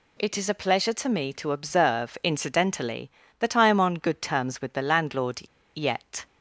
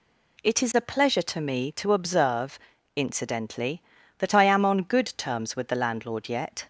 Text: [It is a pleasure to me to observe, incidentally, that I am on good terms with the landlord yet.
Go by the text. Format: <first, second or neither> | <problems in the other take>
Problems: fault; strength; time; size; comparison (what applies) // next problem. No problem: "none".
second | pauses between "landlord" and "yet"; slight; at 5.4 s; 0.33 s long